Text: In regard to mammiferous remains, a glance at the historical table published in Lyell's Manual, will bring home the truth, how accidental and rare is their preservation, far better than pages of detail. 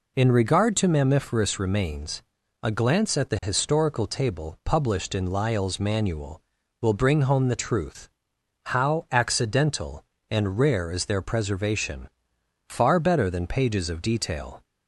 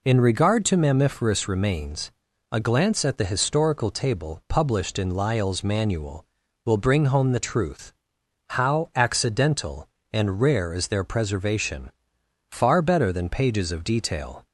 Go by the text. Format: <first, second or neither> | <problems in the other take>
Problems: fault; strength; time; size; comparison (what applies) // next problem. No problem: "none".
neither | none